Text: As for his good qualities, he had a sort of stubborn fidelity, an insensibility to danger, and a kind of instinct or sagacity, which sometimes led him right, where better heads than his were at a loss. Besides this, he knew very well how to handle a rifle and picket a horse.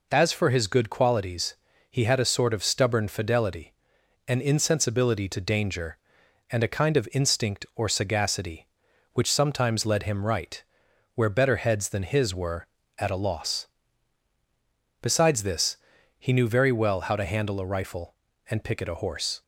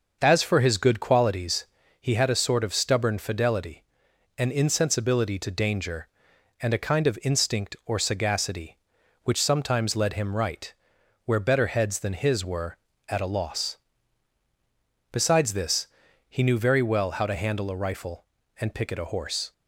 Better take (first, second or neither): first